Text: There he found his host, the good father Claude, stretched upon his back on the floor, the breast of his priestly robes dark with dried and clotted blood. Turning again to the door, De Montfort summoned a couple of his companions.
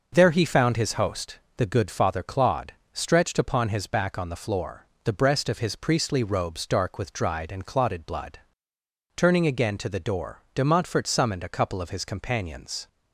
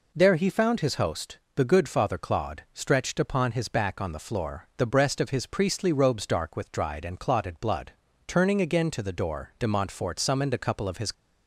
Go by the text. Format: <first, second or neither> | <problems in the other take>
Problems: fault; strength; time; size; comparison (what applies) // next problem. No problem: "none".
first | stops before "companions"; at 11.1 s